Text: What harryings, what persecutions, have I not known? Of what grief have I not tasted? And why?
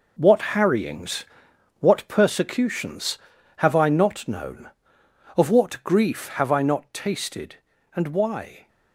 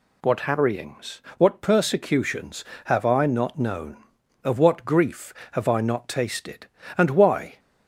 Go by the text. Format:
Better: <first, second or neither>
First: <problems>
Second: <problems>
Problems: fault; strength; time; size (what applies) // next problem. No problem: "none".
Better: second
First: gets quieter; strong; throughout; 9 dB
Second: none